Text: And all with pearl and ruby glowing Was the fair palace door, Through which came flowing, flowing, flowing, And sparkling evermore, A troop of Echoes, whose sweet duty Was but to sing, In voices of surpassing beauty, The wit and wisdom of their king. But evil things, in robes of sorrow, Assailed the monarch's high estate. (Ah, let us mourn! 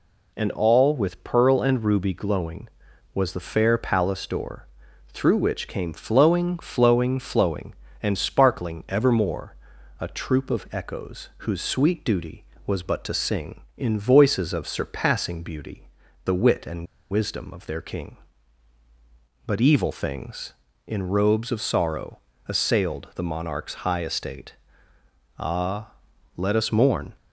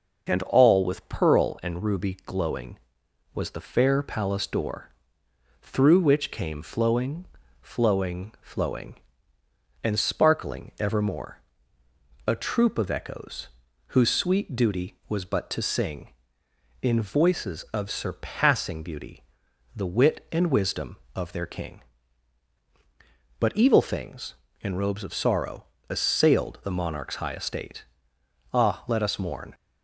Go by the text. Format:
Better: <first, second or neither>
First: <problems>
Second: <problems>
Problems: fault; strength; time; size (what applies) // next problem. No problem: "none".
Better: second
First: pauses between "and" and "wisdom"; slight; at 16.8 s; 0.25 s long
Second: none